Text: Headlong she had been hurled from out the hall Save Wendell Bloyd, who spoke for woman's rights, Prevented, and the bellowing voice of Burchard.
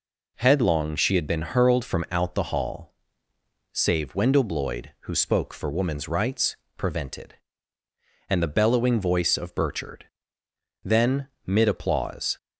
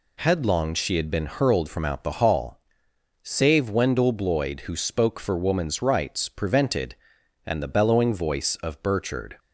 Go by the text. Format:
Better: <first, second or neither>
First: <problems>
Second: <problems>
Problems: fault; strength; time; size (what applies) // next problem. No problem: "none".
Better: second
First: pauses between "hall" and "Save"; noticeable; at 2.9 s; 0.78 s long // goes on to say "Then mid applause"; from 10.8 s on; 1.5 s long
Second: pauses between "hall" and "Save"; noticeable; at 2.5 s; 0.64 s long